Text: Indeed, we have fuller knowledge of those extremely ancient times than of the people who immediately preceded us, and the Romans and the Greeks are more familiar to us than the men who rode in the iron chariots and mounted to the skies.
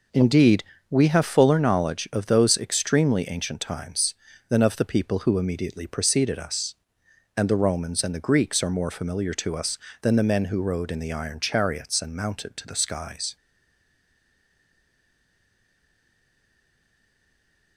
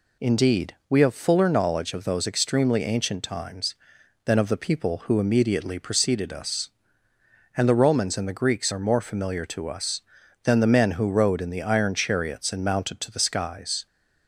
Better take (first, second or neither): second